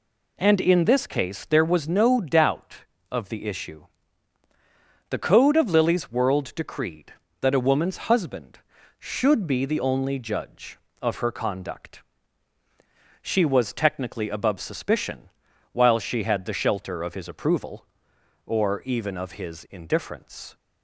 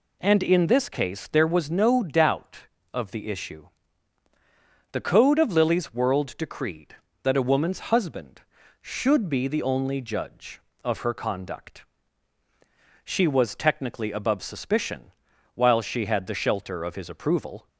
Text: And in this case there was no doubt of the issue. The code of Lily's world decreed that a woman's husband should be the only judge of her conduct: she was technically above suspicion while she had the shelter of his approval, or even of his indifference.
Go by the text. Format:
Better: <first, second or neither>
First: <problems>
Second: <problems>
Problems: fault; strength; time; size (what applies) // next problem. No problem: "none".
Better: first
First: pauses between "suspicion" and "while"; at 15.3 s; 0.42 s long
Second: pauses between "suspicion" and "while"; at 15.1 s; 0.42 s long // stops before "or even of his indifference"; at 17.6 s